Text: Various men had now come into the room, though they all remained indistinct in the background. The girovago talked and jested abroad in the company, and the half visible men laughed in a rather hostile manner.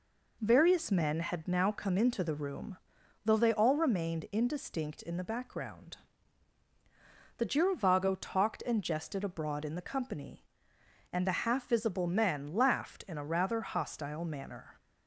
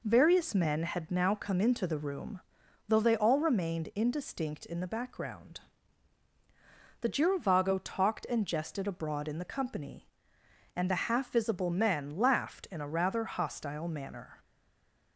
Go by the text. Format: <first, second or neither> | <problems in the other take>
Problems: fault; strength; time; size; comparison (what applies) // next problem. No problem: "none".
first | stays silent after the last word; slight; from 14.4 s on; 0.7 s long